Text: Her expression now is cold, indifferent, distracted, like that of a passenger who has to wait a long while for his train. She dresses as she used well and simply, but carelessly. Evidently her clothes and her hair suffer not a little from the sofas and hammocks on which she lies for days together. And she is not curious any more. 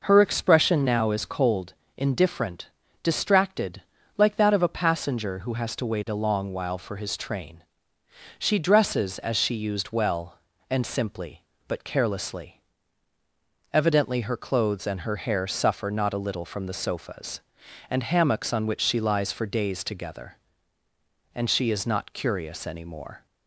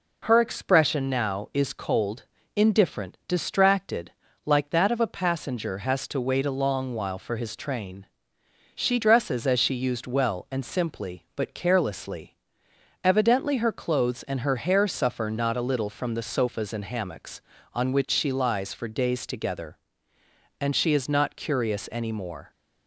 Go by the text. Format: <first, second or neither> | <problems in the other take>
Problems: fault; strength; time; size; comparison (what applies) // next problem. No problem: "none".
first | skips "who"; at 5.7 s